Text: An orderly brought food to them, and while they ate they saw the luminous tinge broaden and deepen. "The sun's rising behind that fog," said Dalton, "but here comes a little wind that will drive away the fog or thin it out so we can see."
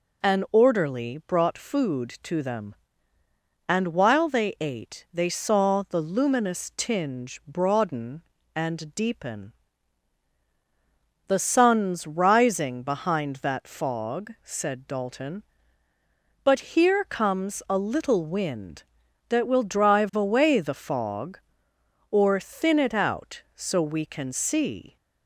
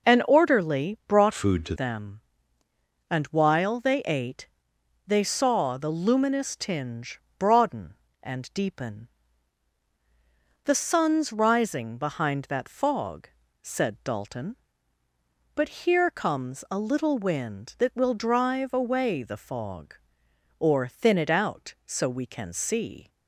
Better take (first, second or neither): first